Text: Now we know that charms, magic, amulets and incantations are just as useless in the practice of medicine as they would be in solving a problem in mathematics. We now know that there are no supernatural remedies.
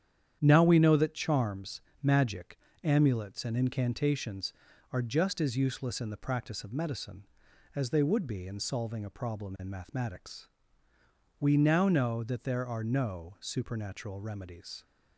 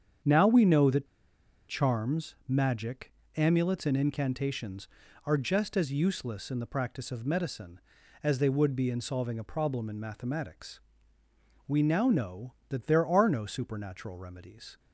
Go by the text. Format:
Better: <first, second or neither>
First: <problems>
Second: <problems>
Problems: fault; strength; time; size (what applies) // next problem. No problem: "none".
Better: first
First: starts louder than the rest; strong; until 1.4 s; 9.5 dB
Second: starts louder than the rest; strong; until 1.8 s; 8 dB // pauses between "that" and "charms"; noticeable; at 1.0 s; 0.62 s long